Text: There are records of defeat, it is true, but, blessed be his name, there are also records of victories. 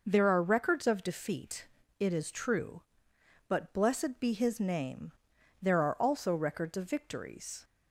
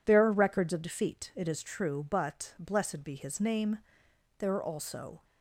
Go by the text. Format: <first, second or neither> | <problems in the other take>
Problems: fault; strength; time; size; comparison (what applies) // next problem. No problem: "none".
first | stops before "records of victories"; at 5.2 s